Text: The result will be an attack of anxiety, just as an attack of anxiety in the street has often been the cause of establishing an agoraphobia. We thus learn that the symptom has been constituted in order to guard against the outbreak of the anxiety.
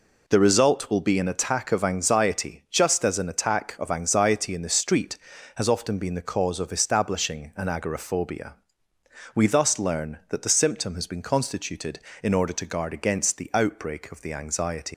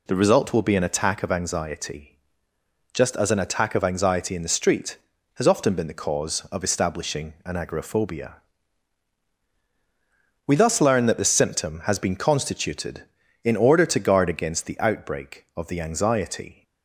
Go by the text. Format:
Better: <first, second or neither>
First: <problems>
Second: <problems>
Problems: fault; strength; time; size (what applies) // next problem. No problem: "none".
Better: second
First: leaves "anxiety" unfinished; at 14.9 s; 120 ms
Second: none